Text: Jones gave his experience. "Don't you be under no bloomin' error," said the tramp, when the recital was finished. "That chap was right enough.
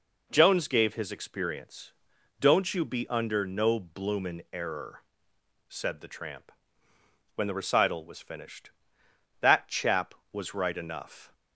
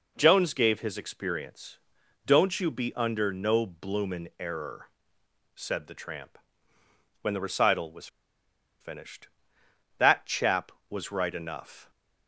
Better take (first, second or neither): first